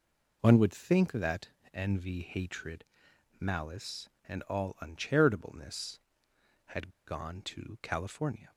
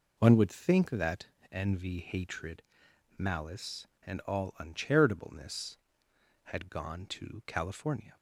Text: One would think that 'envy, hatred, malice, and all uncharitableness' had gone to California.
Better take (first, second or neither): second